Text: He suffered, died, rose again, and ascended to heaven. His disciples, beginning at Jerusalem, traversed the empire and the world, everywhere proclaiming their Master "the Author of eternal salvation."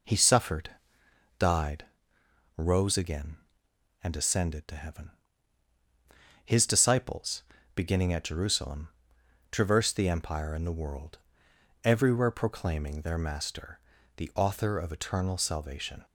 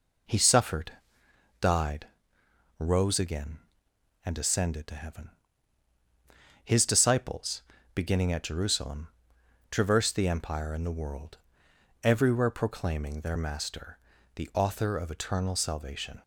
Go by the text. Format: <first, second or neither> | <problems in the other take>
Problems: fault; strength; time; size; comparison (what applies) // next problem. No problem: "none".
neither | pauses between "Master" and "the"; slight; the same in both